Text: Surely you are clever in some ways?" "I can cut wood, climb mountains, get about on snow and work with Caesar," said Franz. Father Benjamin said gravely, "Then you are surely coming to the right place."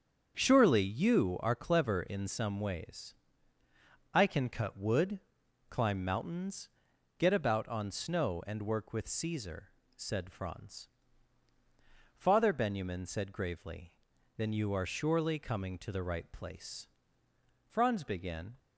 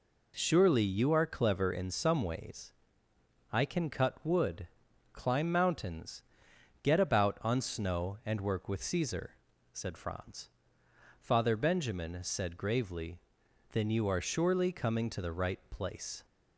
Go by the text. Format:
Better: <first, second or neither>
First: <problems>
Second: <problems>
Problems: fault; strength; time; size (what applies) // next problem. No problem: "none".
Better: second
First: starts louder than the rest; strong; until 1.3 s; 7.5 dB // goes on to say "Franz began"; noticeable; from 17.6 s on; 0.92 s long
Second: none